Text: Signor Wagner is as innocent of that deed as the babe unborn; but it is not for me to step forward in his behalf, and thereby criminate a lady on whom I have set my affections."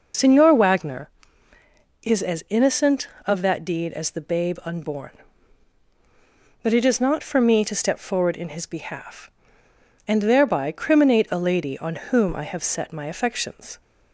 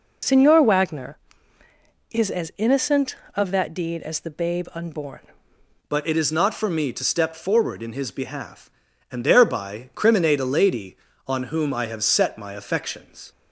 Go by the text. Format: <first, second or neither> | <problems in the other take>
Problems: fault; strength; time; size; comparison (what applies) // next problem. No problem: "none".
first | changes voice at "but"; from 5.8 s on; 7.5 s long